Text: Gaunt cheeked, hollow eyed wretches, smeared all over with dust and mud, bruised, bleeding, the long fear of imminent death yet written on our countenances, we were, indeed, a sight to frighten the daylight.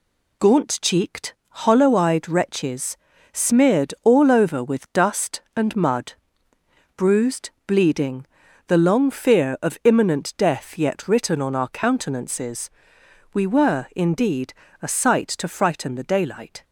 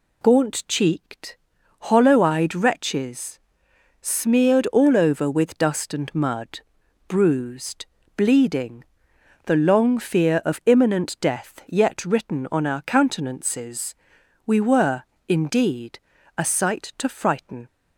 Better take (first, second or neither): first